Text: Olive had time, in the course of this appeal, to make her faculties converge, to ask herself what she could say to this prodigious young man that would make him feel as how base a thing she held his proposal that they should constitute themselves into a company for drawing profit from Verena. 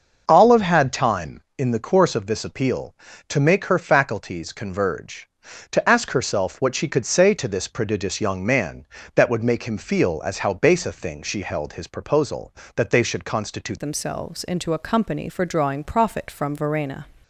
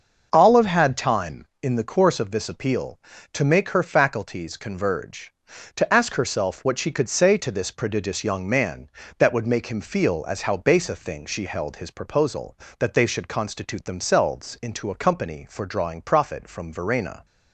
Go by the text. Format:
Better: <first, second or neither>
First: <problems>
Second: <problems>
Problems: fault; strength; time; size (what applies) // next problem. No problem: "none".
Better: second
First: starts louder than the rest; until 1.2 s; 6 dB // changes voice at "themselves"; from 13.8 s on; 3.2 s long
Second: starts louder than the rest; until 1.3 s; 6 dB